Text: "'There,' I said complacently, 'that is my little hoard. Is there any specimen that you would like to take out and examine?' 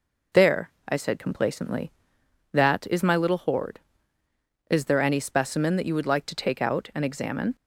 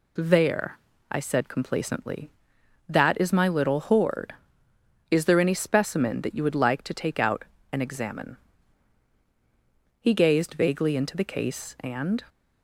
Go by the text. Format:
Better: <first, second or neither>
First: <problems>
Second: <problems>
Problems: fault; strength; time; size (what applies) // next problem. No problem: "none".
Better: first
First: none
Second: goes on to say "He gazed vaguely into the case and"; strong; from 10.0 s on; 2.2 s long